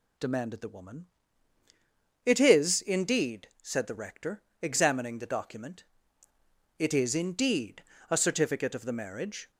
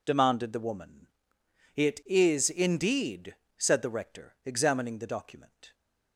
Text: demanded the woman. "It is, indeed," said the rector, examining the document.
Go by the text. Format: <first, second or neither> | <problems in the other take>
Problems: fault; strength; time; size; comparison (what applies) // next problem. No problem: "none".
second | goes on to say "It is indeed a certificate of the marriage"; strong; from 6.7 s on; 2.7 s long